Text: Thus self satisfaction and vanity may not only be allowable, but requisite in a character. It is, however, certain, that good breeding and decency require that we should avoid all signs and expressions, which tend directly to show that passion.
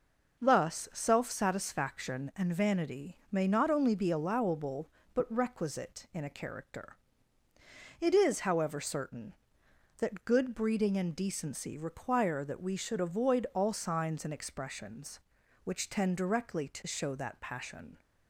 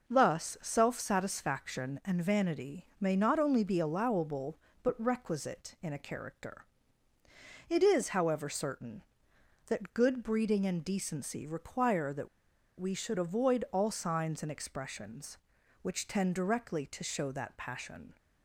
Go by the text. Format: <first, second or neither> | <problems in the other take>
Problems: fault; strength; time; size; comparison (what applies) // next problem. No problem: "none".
first | pauses between "that" and "we"; noticeable; at 12.2 s; 0.51 s long